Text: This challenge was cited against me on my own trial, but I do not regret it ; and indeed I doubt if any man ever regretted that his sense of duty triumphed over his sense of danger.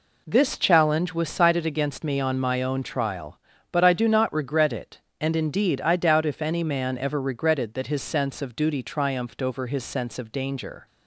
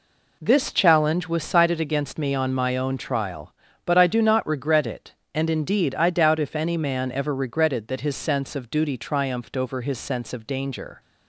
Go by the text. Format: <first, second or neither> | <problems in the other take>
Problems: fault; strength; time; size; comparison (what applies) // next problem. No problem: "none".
neither | none